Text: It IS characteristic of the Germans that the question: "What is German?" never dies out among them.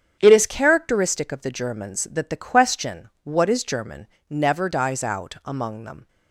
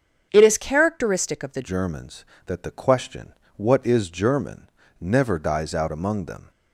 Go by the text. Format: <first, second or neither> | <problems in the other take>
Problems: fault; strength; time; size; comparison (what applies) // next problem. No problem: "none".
first | starts louder than the rest; strong; until 1.3 s; 8 dB; strong in the first // changes voice at "Germans"; from 1.6 s on; 4.9 s long